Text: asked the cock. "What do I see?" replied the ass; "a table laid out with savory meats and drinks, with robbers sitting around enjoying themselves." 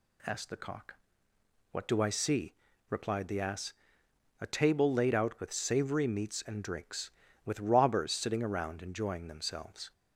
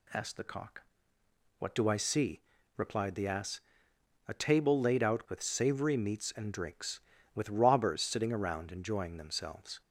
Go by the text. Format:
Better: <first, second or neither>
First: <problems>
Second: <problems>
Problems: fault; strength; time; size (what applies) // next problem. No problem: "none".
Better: neither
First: none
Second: none